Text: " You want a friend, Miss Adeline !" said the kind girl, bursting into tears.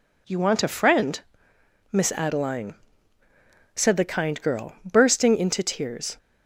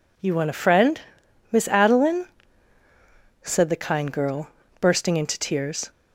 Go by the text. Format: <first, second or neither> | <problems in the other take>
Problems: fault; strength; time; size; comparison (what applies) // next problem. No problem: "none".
neither | none